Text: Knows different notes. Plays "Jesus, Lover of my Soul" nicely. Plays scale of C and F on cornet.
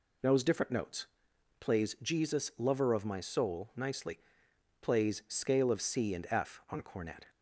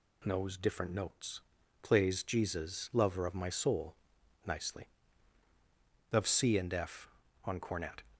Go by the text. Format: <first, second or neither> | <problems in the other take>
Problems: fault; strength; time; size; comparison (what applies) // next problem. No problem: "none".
first | pauses between "Soul" and "nicely"; noticeable; at 3.9 s; 0.50 s long // skips "Plays scale"; at 5.4 s